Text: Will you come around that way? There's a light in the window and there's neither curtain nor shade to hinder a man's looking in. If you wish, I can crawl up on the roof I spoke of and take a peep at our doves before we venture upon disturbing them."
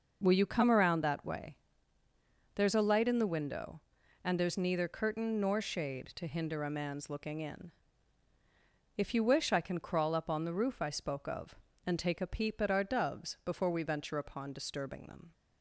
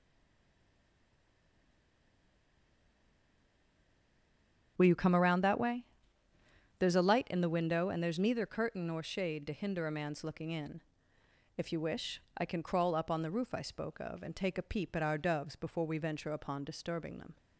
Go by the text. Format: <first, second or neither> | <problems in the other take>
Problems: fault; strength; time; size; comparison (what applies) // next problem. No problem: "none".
first | stays silent before the first word; strong; until 4.7 s; 4.7 s long // starts louder than the rest; strong; until 5.7 s; 8 dB